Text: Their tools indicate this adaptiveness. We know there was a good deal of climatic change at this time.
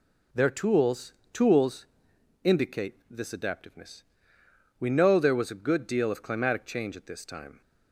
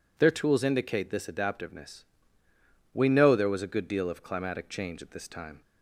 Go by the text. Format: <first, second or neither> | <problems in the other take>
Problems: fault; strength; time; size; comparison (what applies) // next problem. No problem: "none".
second | says "tools" twice; at 1.3 s